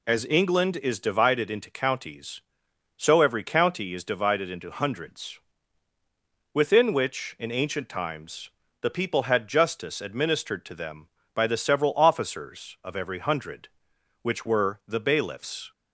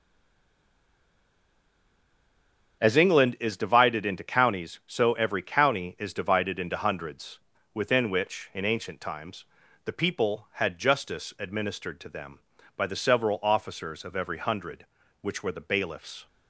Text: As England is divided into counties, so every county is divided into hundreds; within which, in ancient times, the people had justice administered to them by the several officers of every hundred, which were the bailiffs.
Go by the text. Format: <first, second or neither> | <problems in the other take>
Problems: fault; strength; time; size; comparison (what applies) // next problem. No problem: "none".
first | stays silent before the first word; strong; until 2.8 s; 2.8 s long // starts louder than the rest; strong; until 3.8 s; 7.5 dB